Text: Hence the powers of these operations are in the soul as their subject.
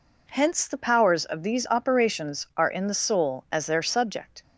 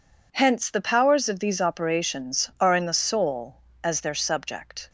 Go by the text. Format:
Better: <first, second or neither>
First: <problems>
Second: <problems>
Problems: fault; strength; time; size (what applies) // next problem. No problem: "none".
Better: neither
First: none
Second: none